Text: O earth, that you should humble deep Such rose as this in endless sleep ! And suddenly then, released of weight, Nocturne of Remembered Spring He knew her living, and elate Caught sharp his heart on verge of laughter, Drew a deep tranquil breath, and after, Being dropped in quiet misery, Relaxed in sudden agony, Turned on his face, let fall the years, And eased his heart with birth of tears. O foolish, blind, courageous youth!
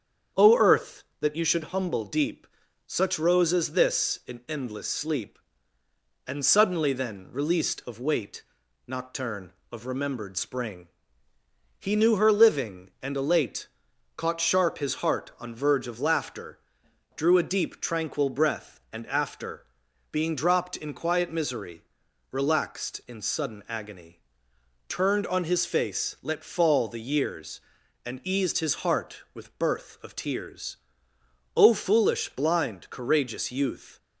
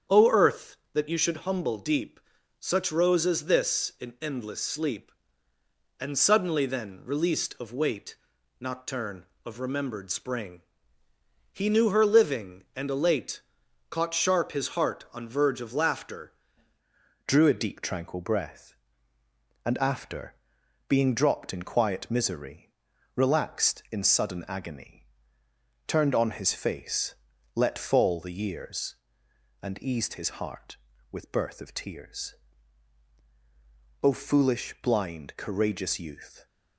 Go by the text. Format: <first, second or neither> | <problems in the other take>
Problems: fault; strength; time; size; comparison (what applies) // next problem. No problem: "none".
first | starts louder than the rest; strong; until 1.2 s; 8 dB; strong in the first // pauses between "deep" and "Such"; at 2.1 s; 0.40 s long; also in the first // pauses between "Spring" and "He"; noticeable; at 10.6 s; 0.90 s long; noticeable in the first // pauses between "elate" and "Caught"; noticeable; at 13.4 s; 0.48 s long; noticeable in the first // changes voice at "Drew"; from 17.2 s on; 19.2 s long